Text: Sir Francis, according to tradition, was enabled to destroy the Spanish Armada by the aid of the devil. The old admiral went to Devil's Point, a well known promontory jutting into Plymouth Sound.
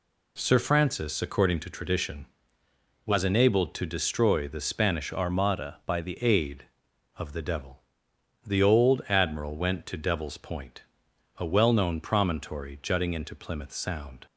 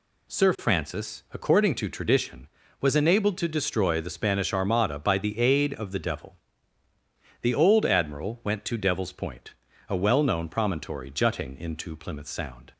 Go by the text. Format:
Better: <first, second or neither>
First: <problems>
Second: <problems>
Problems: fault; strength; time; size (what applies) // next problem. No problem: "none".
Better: second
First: changes voice from "Armada" to "the"; from 5.1 to 6.1 s; 1.0 s long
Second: none